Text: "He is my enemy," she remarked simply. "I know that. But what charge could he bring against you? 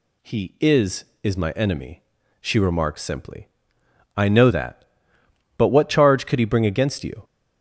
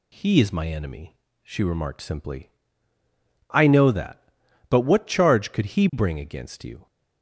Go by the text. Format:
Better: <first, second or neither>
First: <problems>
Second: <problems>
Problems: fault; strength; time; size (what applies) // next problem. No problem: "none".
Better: second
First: says "is" twice; at 1.2 s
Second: none